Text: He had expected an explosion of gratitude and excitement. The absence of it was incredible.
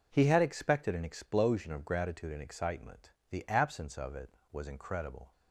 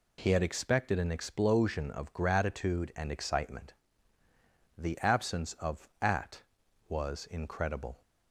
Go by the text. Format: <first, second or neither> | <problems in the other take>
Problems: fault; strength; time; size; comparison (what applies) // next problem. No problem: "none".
first | says "at" for "it"; at 6.0 s